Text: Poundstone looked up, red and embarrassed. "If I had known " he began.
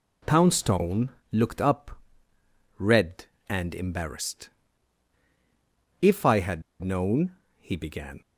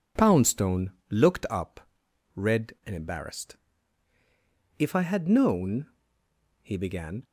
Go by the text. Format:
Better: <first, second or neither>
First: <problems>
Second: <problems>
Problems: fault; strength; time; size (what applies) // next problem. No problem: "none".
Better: second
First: pauses between "Poundstone" and "looked"; slight; at 1.0 s; 0.24 s long // pauses between "had" and "known"; slight; at 6.6 s; 0.20 s long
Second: pauses between "Poundstone" and "looked"; slight; at 0.9 s; 0.18 s long